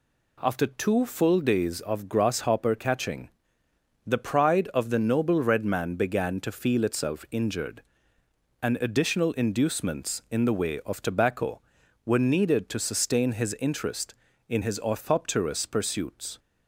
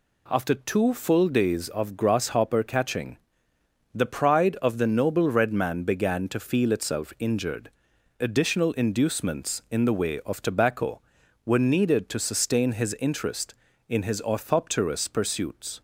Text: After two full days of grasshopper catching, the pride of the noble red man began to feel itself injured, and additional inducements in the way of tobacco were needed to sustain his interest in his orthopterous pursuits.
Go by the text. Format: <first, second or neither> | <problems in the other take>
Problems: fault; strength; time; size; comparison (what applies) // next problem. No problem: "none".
first | skips "and"; at 7.9 s